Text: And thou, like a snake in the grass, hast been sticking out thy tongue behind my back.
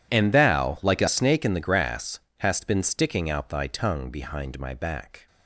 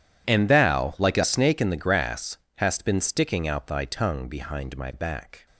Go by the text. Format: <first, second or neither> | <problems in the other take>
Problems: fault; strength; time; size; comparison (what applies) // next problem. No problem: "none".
neither | none